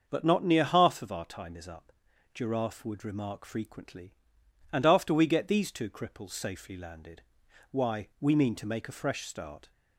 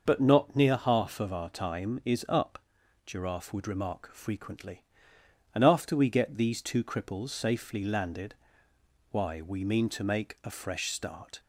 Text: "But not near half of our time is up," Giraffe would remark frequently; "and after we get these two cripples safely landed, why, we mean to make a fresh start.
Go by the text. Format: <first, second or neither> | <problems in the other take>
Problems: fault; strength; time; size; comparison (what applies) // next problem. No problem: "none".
first | loses the start of "But"; at 0.0 s; 30 ms // starts louder than the rest; until 1.0 s; 6 dB; also in the first